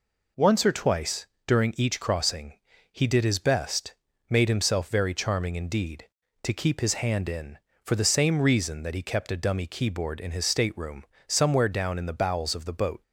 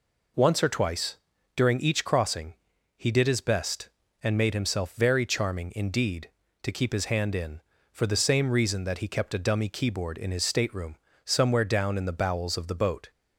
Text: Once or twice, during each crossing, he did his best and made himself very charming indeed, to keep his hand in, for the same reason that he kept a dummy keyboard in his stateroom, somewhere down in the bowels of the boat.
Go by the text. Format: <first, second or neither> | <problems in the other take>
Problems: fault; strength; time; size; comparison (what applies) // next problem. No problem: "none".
second | skips "and"; at 4.1 s